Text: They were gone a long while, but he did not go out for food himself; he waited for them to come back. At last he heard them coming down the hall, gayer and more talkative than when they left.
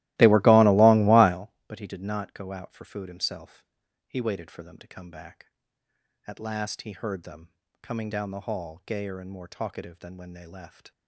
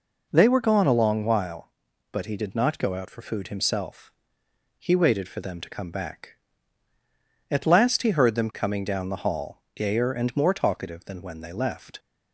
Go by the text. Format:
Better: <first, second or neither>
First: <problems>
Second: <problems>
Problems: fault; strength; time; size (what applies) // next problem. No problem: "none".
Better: second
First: starts louder than the rest; strong; until 1.4 s; 17.5 dB // pauses between "them" and "coming"; slight; at 7.4 s; 0.32 s long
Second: none